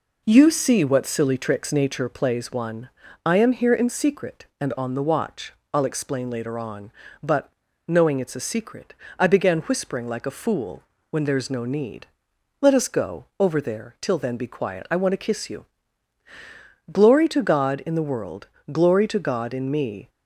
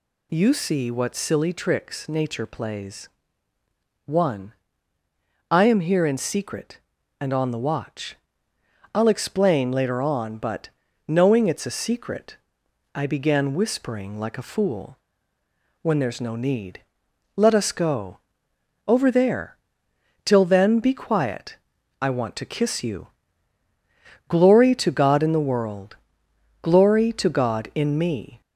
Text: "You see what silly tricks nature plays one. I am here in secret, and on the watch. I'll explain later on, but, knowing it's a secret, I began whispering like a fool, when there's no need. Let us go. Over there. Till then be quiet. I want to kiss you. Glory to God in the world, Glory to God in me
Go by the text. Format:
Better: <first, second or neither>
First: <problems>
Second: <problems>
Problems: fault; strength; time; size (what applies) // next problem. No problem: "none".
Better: first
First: none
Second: gets louder; slight; throughout; 3 dB // pauses between "plays" and "one"; noticeable; at 3.0 s; 0.98 s long